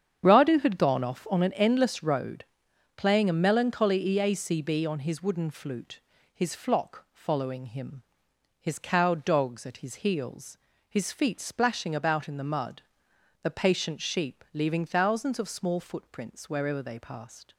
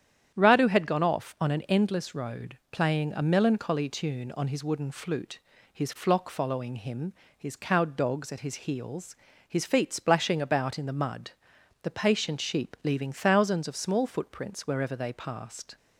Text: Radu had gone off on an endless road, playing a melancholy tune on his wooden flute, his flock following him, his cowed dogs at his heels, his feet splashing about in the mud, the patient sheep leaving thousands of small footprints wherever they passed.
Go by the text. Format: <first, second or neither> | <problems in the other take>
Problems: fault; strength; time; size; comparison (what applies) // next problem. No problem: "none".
second | starts louder than the rest; strong; until 1.2 s; 8 dB; strong in the second // says "eacb" for "tune"; at 4.0 s